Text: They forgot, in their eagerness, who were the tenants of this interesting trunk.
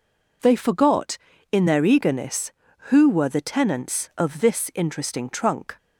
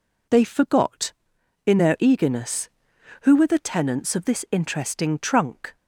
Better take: neither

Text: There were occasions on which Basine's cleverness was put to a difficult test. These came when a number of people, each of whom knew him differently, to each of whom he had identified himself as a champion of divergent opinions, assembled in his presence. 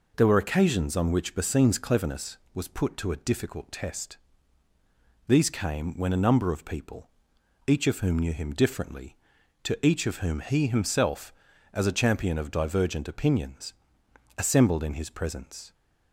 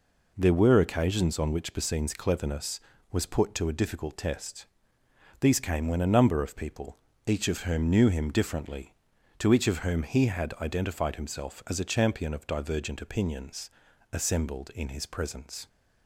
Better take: second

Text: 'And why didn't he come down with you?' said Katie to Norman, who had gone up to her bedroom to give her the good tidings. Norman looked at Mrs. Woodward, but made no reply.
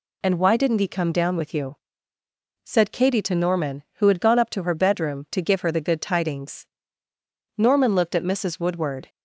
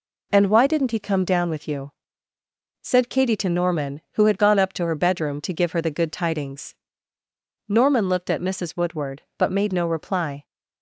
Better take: second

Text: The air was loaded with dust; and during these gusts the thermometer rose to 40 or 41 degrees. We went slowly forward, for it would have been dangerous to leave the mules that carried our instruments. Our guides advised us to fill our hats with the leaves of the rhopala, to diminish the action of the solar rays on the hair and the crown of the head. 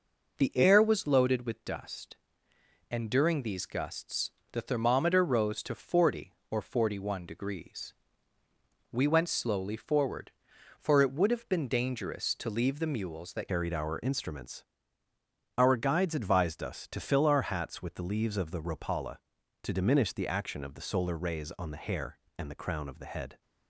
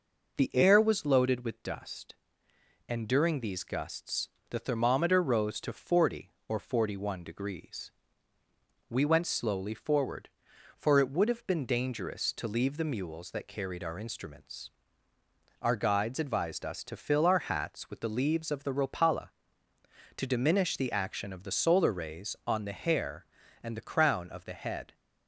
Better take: second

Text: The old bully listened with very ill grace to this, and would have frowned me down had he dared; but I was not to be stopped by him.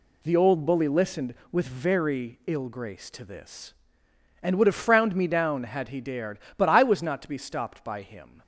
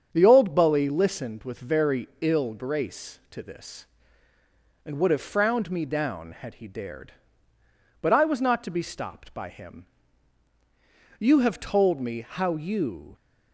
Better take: first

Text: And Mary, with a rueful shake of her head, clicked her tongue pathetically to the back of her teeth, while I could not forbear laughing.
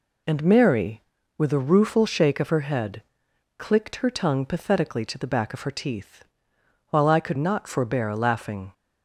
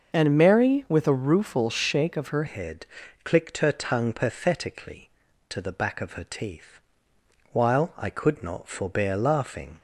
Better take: first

